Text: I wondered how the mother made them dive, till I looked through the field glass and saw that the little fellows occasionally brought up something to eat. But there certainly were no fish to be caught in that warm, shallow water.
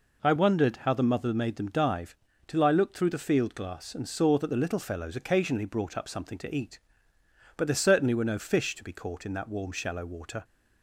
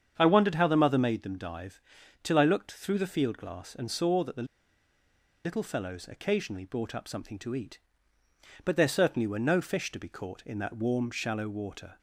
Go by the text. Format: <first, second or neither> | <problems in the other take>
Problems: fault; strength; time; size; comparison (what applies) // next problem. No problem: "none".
first | starts louder than the rest; strong; until 1.1 s; 8 dB // pauses between "the" and "little"; at 4.4 s; 1.0 s long